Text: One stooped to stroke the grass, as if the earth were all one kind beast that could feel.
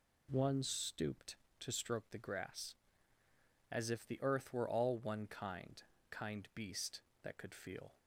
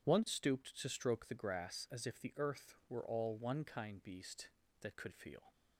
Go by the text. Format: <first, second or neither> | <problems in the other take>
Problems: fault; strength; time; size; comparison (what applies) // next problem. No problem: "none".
second | says "kind" twice; at 6.1 s